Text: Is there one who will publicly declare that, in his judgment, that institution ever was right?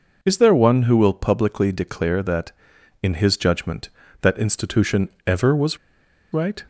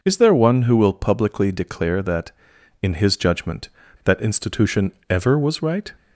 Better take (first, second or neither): second